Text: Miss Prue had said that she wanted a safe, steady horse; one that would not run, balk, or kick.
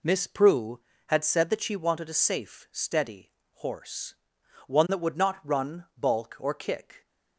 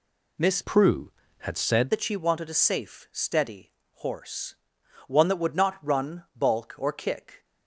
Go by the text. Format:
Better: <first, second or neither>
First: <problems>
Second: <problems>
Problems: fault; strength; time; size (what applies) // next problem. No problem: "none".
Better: first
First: pauses between "steady" and "horse"; slight; at 3.2 s; 0.24 s long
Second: changes voice from "Prue" to "said"; from 0.6 to 1.8 s; 1.2 s long // pauses between "steady" and "horse"; slight; at 3.7 s; 0.24 s long